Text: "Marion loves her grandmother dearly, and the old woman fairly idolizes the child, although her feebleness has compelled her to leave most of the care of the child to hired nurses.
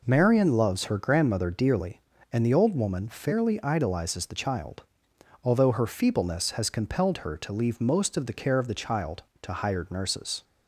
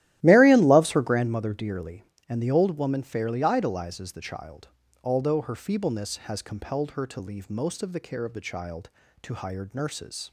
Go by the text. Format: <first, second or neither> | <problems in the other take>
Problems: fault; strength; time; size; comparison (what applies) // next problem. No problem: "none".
first | starts louder than the rest; strong; until 1.4 s; 14 dB